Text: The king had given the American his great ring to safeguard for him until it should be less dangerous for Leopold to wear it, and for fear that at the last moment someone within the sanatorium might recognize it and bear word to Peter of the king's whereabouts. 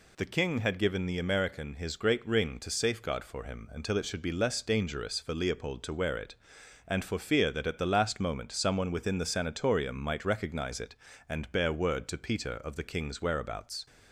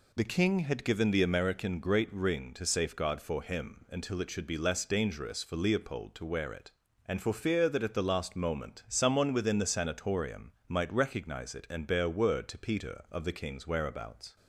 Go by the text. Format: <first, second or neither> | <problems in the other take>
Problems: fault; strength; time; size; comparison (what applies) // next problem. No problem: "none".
first | skips "his"; at 1.7 s // pauses between "sanatorium" and "might"; slight; at 10.5 s; 0.16 s long